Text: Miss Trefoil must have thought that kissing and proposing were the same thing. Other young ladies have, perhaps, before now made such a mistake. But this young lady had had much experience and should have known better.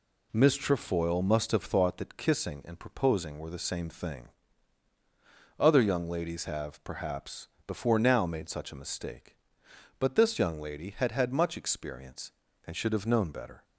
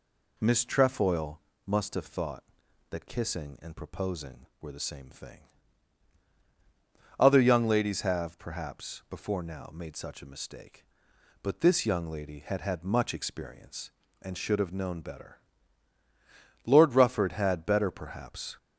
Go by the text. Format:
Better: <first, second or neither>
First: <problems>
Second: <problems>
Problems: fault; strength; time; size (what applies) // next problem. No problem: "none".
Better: first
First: none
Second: pauses between "Trefoil" and "must"; slight; at 1.4 s; 0.24 s long // goes on to say "Lord Rufford had better perhaps"; strong; from 16.6 s on; 1.9 s long